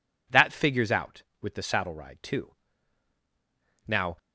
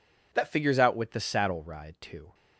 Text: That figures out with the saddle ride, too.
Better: second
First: goes on to say "Now"; slight; from 3.8 s on; 0.30 s long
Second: none

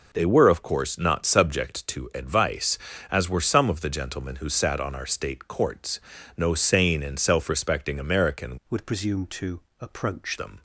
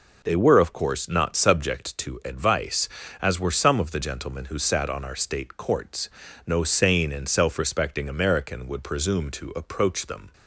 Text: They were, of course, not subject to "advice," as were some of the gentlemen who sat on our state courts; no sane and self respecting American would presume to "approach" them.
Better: second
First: changes voice from "would" to "approach"; from 8.6 to 10.3 s; 1.7 s long // pauses between "to" and "approach"; slight; at 9.6 s; 0.20 s long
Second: none

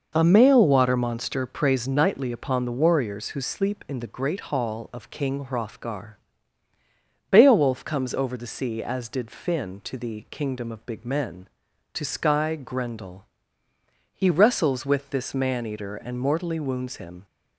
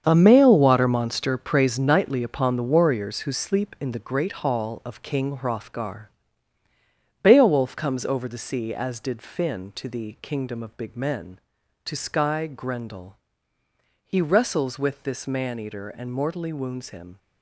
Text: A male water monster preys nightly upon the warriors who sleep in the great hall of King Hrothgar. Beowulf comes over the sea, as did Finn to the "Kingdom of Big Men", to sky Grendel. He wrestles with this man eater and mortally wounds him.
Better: first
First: none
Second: gets quieter; strong; throughout; 11 dB

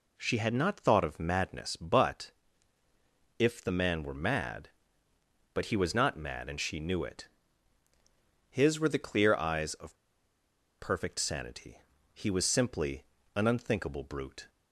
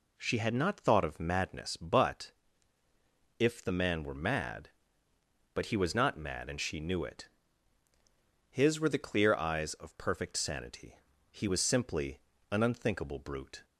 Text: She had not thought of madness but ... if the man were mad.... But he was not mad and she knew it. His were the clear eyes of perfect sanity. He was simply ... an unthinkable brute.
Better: second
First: pauses between "of" and "perfect"; noticeable; at 9.9 s; 0.82 s long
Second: none

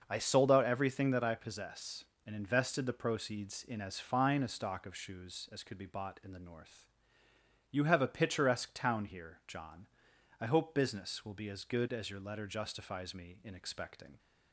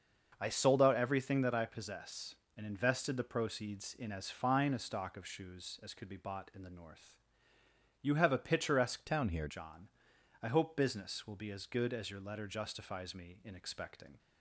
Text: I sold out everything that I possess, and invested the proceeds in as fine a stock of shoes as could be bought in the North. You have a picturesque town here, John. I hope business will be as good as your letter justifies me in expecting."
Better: first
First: starts louder than the rest; noticeable; until 1.0 s; 6 dB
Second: starts louder than the rest; until 1.4 s; 6 dB // changes voice from "town" to "here"; from 9.0 to 9.4 s; 0.4 s long

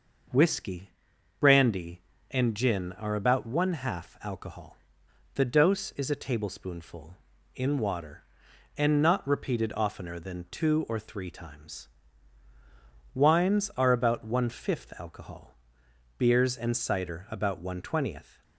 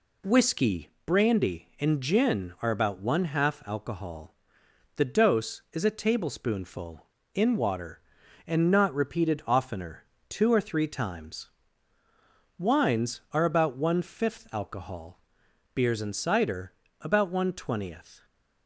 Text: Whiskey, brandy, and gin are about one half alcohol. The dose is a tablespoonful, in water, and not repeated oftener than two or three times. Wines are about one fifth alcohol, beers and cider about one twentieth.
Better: first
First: none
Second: skips "than"; at 10.1 s // pauses between "cider" and "about"; slight; at 16.7 s; 0.30 s long

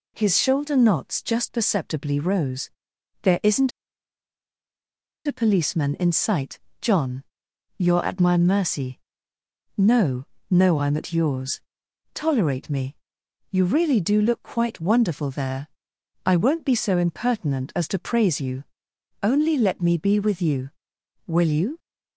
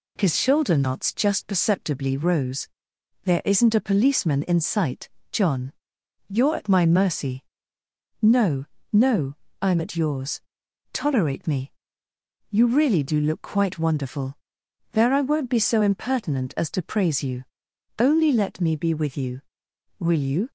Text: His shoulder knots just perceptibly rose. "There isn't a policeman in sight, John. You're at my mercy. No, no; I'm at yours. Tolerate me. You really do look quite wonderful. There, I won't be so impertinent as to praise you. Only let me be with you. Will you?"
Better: second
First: pauses between "isn't" and "a"; strong; at 3.7 s; 1.5 s long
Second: none

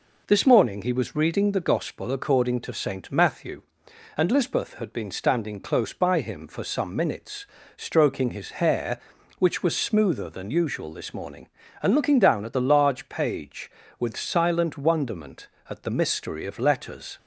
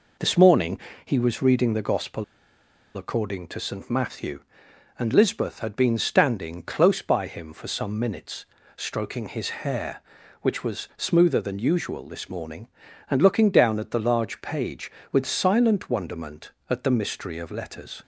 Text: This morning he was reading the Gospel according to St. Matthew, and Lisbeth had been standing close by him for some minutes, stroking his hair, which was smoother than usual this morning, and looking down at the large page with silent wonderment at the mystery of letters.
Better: first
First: none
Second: pauses between "morning" and "he"; slight; at 0.8 s; 0.24 s long // pauses between "Gospel" and "according"; noticeable; at 2.2 s; 0.72 s long

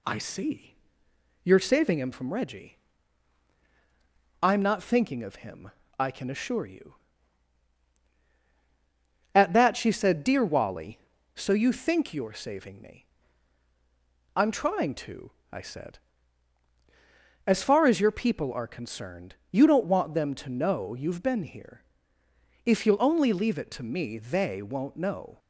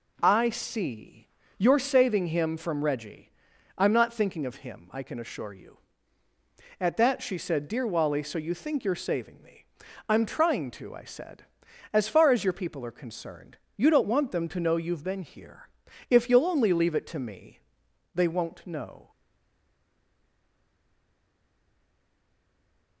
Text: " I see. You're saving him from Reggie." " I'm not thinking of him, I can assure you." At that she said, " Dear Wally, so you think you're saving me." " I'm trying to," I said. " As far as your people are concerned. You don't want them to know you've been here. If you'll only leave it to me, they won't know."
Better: first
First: none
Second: stays silent after the last word; strong; from 19.1 s on; 3.9 s long

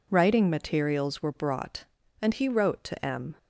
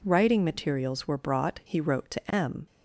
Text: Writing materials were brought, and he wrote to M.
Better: first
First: none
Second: skips "and"; at 1.6 s

